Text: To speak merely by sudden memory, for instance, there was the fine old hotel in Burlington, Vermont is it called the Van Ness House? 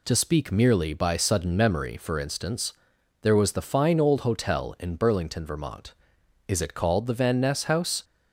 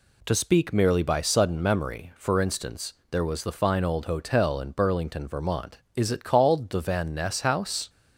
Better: neither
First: none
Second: none

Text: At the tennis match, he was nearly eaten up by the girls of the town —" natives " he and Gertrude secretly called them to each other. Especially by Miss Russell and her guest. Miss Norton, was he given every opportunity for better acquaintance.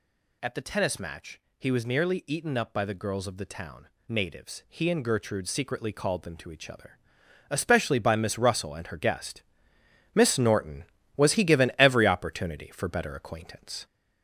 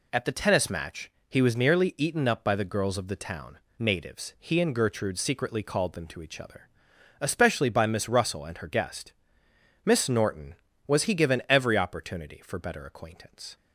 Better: second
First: gets louder; noticeable; throughout; 4.5 dB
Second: none

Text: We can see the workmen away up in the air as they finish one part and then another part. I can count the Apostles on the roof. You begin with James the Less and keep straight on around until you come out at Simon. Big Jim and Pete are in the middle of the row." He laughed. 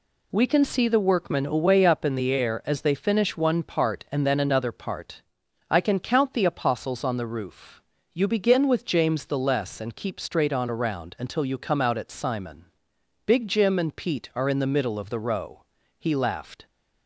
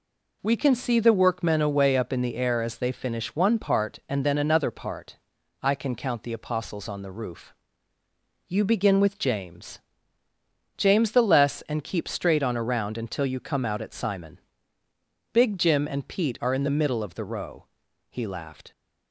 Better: first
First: none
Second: says "James" twice; at 10.7 s

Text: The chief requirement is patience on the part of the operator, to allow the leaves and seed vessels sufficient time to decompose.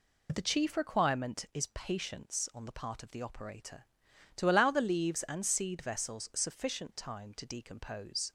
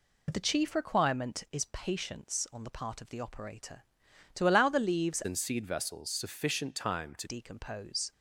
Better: first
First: none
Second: changes voice from "and" to "to"; from 5.2 to 7.2 s; 2.0 s long

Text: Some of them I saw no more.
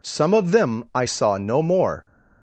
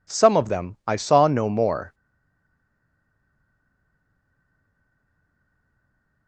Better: first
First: none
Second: stays silent after the last word; strong; from 1.9 s on; 4.3 s long

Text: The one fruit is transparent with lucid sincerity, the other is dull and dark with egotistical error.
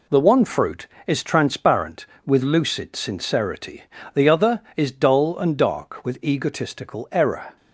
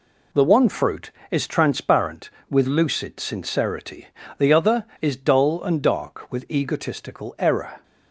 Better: neither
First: none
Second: none

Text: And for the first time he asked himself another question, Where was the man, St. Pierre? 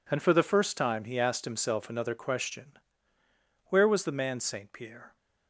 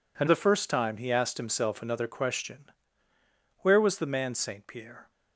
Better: first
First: none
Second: skips "for"; at 0.2 s

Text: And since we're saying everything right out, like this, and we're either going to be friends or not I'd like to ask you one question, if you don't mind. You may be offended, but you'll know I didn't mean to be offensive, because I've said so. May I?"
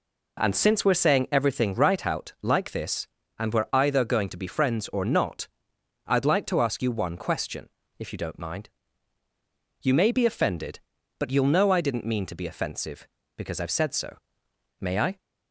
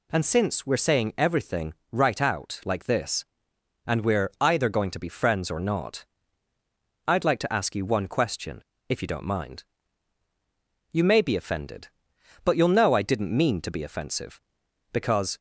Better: first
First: pauses between "not" and "I'd"; noticeable; at 5.4 s; 0.62 s long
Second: pauses between "everything" and "right"; slight; at 1.7 s; 0.18 s long // pauses between "not" and "I'd"; at 6.0 s; 1.0 s long // stops before "I've said so May I"; at 15.3 s

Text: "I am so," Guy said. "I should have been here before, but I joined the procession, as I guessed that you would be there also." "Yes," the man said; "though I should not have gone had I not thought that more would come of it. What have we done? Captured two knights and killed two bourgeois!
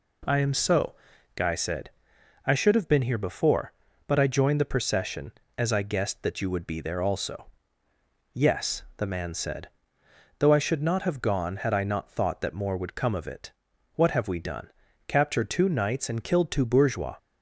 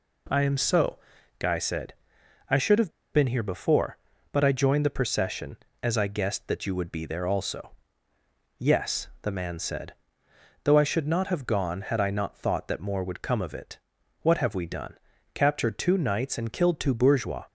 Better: first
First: none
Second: pauses between "have" and "been"; slight; at 2.9 s; 0.21 s long

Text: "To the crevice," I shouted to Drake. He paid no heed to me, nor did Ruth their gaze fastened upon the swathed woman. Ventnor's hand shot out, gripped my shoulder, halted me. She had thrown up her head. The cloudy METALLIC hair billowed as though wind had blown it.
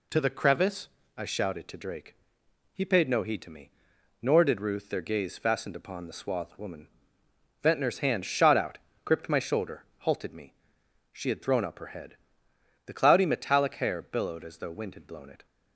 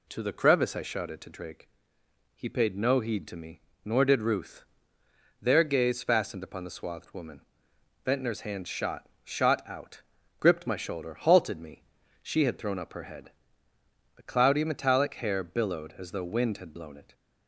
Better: first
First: none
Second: pauses between "Ruth" and "their"; noticeable; at 4.6 s; 0.76 s long // says "shot" twice; at 9.2 s

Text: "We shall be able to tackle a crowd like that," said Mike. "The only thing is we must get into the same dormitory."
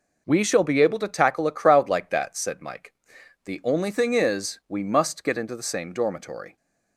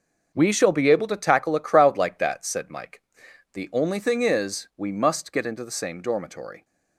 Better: first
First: none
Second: gets quieter; strong; throughout; 10.5 dB

